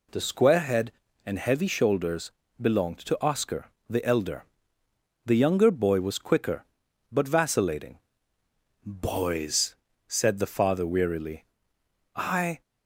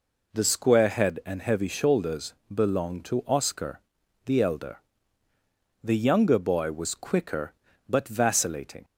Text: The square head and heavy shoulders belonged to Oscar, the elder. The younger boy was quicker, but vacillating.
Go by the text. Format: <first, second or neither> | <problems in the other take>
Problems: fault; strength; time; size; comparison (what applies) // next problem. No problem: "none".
second | pauses between "shoulders" and "belonged"; slight; at 2.3 s; 0.28 s long // goes on to say "Boys said the father wearily I"; strong; from 8.8 s on; 3.7 s long